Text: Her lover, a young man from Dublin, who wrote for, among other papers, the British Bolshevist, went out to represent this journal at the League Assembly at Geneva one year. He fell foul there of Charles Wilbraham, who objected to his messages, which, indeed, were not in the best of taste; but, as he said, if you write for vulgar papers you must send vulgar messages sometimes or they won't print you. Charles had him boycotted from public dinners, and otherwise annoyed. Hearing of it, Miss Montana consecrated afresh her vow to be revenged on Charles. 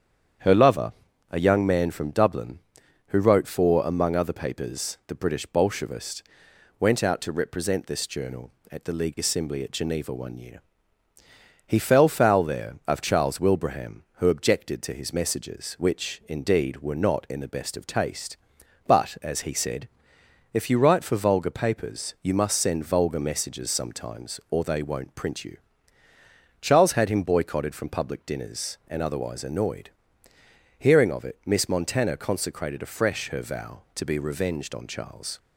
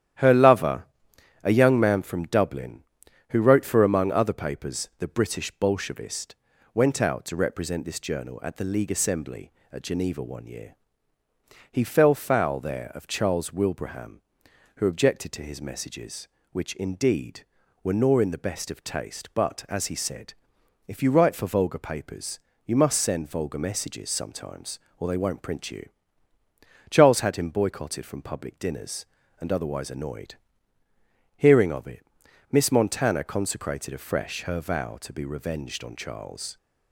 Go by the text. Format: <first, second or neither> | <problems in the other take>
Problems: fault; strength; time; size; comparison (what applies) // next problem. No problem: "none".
first | starts louder than the rest; strong; until 1.7 s; 11.5 dB; strong in the first // says "nor" for "not"; at 17.9 s // pauses between "papers" and "you"; slight; at 22.3 s; 0.26 s long